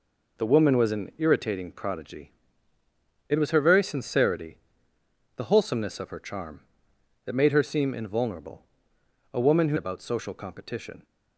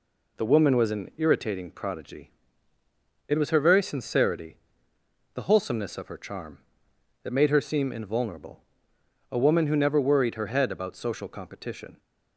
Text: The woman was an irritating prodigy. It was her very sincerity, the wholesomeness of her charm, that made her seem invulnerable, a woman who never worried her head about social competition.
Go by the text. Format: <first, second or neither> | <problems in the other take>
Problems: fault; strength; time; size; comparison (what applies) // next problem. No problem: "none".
second | skips "never worried her head"; at 9.7 s